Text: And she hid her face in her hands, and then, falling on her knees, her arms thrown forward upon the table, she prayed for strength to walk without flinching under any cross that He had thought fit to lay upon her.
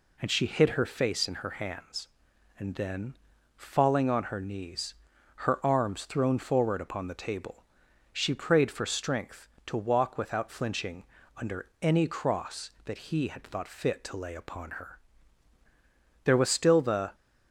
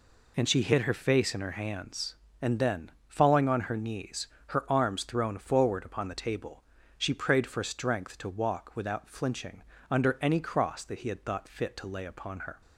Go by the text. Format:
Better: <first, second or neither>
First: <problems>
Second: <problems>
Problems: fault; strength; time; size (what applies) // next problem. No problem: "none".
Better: second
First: pauses between "flinching" and "under"; slight; at 11.0 s; 0.34 s long // pauses between "under" and "any"; slight; at 11.6 s; 0.16 s long // goes on to say "There was still the"; noticeable; from 16.2 s on; 0.92 s long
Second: pauses between "flinching" and "under"; slight; at 9.6 s; 0.26 s long